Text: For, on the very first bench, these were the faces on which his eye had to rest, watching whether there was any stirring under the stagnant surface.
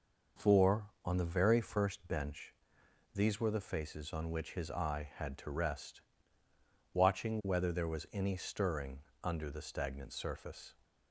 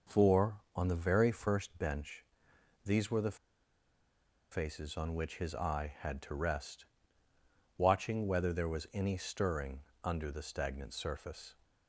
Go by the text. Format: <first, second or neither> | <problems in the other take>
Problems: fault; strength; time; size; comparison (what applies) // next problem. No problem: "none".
first | pauses between "the" and "faces"; at 3.3 s; 1.1 s long // pauses between "stirring" and "under"; slight; at 9.8 s; 0.20 s long; slight in the first